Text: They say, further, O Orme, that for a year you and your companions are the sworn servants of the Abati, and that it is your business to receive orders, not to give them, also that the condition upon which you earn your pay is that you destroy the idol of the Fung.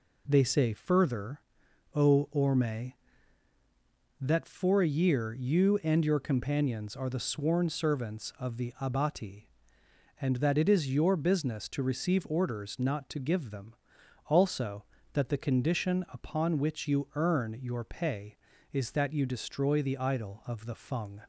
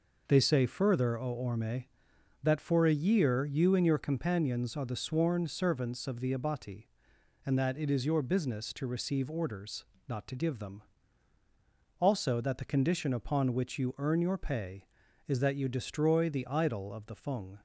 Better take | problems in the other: neither | none

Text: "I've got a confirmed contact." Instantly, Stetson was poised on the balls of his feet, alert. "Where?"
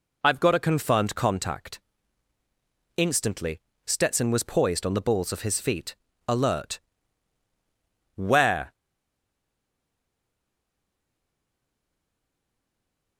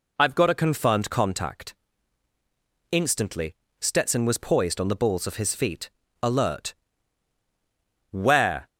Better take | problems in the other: second | stays silent after the last word; strong; from 8.7 s on; 4.4 s long

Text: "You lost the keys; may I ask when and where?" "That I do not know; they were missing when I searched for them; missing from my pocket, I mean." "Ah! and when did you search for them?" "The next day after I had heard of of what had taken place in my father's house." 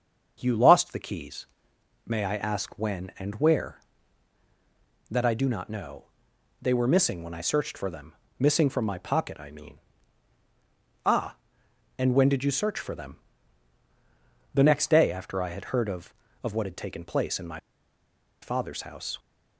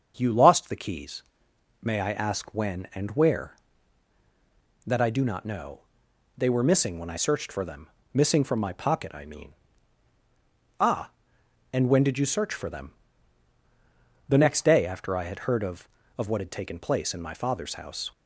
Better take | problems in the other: second | starts louder than the rest; until 1.4 s; 7 dB; also in the second // pauses between "my" and "father's"; noticeable; at 17.5 s; 0.83 s long

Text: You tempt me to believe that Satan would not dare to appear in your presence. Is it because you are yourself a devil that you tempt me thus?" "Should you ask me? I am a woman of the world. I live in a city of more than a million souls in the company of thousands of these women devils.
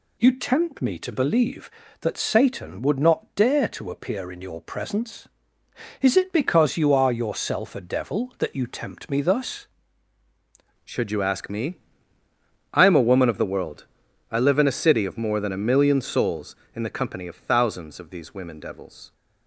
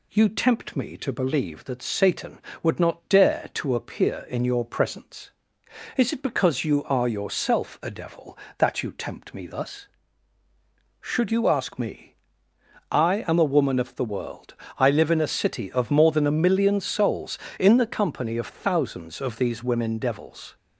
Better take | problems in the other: second | changes voice at "Should"; from 10.8 s on; 8.3 s long

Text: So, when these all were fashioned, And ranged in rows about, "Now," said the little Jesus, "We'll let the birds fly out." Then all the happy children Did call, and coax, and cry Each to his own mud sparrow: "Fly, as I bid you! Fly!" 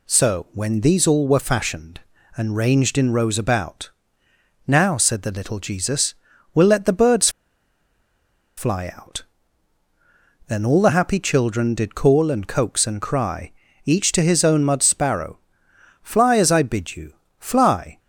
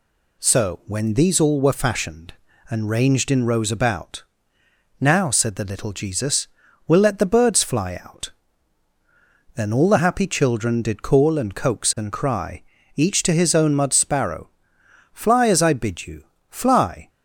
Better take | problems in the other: second | pauses between "birds" and "fly"; strong; at 7.2 s; 1.2 s long // pauses between "cry" and "Each"; slight; at 13.5 s; 0.34 s long; slight in the second

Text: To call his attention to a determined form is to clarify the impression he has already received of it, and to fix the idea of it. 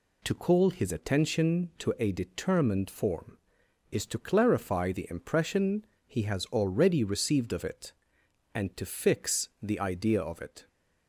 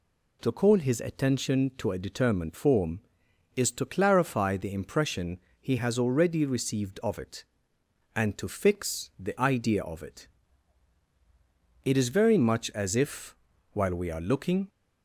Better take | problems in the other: first | pauses between "impression" and "he"; slight; at 5.3 s; 0.22 s long; slight in the first // goes on to say "It is very much as if while we are looking"; strong; from 11.8 s on; 2.8 s long

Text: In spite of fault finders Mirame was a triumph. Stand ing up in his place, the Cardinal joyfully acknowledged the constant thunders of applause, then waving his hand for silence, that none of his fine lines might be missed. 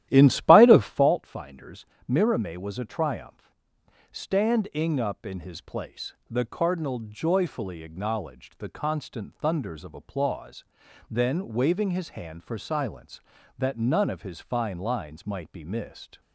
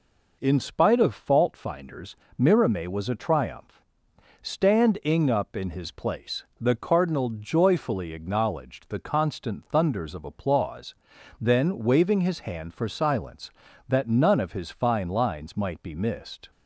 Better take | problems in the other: second | starts louder than the rest; strong; until 1.2 s; 13 dB // pauses between "finders" and "Mirame"; slight; at 1.8 s; 0.24 s long; slight in the second

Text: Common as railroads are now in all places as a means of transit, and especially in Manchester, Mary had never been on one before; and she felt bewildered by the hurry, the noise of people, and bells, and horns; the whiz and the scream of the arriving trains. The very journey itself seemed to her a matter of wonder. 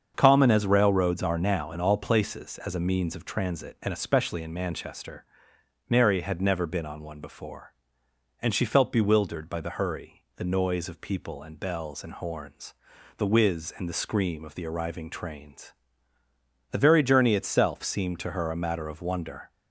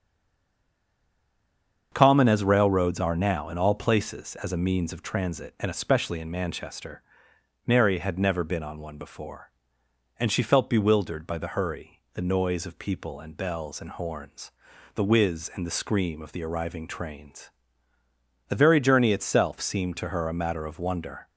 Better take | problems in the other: first | stays silent before the first word; noticeable; until 1.9 s; 1.9 s long // starts louder than the rest; until 2.9 s; 7 dB; also in the first

